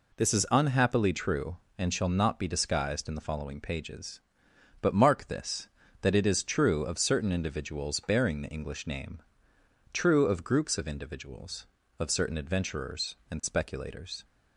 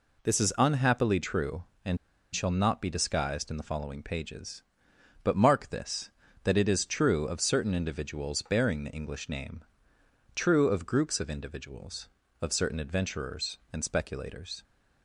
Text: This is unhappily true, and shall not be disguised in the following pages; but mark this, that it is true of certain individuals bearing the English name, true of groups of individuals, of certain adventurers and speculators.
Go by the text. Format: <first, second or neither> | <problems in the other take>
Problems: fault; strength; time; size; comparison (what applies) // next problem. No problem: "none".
first | pauses between "and" and "shall"; at 1.9 s; 0.36 s long